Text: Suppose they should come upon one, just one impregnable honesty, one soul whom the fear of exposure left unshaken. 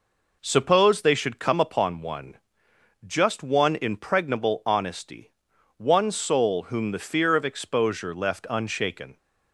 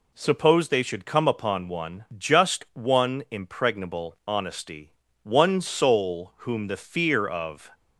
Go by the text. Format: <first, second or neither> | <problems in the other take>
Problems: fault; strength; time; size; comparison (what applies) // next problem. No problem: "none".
first | stops before "exposure left unshaken"; at 7.7 s